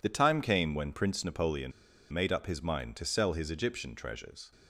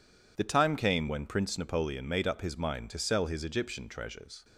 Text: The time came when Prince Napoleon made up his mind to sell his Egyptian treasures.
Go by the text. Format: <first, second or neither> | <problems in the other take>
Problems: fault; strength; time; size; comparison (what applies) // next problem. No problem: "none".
second | pauses between "Napoleon" and "made"; at 1.7 s; 0.41 s long